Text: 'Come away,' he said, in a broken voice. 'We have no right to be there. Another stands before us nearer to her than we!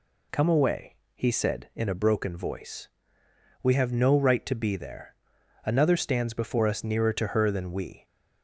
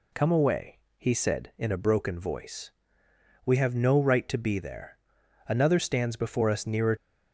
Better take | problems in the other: first | stops before "to her than we"; at 6.9 s

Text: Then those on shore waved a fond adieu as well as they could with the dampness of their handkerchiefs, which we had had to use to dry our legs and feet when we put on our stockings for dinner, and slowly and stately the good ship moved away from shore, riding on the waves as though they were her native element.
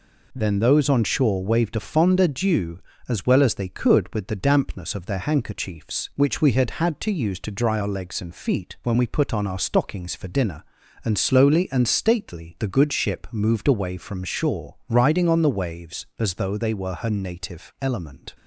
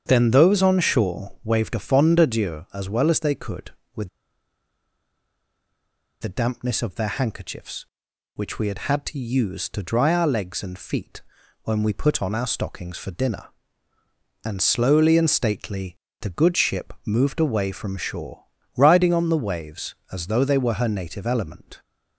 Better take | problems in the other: first | starts louder than the rest; strong; until 1.0 s; 7.5 dB // pauses between "with" and "the"; strong; at 4.0 s; 2.1 s long // pauses between "feet" and "when"; at 11.2 s; 0.42 s long // pauses between "stately" and "the"; slight; at 15.9 s; 0.24 s long

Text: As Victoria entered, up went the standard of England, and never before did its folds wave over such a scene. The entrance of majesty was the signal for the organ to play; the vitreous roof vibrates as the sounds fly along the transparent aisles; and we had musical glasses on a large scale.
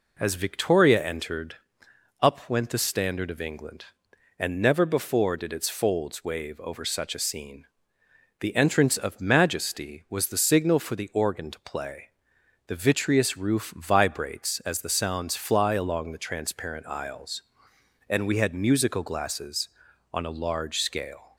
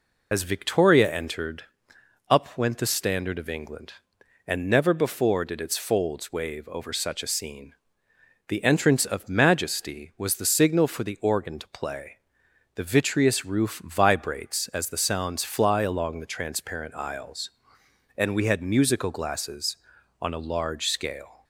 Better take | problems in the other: first | loses the start of "As"; at 0.3 s; 45 ms

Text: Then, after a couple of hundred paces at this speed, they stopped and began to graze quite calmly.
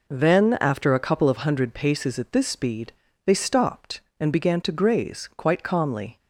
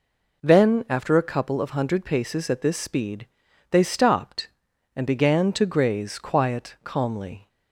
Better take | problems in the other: first | says "quiet" for "quite"; at 6.1 s

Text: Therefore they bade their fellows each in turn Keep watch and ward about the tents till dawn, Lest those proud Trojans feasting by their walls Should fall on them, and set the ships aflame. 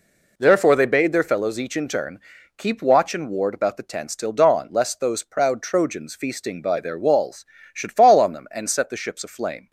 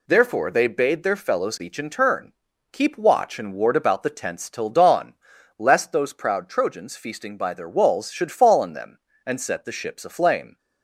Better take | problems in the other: neither | pauses between "turn" and "Keep"; the same in both

